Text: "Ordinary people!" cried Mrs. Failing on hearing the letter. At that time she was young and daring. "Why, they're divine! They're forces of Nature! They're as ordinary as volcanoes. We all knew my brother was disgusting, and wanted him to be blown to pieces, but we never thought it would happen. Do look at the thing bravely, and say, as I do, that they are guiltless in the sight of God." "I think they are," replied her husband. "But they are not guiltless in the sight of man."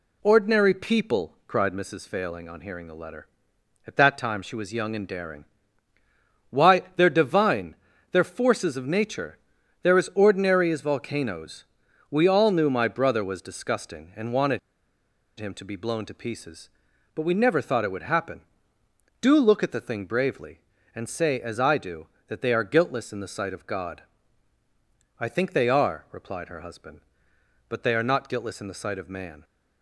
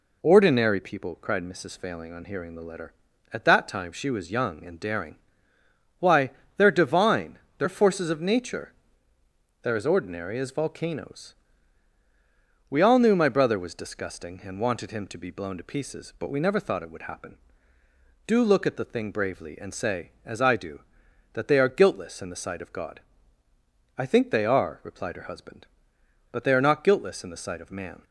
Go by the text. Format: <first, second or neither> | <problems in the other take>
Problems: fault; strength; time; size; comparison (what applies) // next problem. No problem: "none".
second | pauses between "wanted" and "him"; noticeable; at 14.5 s; 0.78 s long